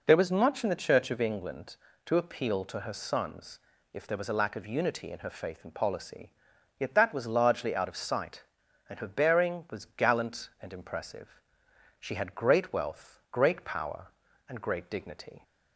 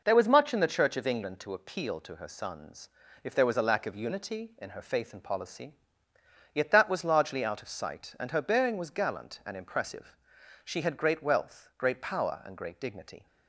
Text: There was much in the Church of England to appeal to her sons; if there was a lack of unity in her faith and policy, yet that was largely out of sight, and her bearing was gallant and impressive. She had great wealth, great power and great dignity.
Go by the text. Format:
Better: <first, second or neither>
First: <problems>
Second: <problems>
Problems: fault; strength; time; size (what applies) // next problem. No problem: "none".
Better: neither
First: none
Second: none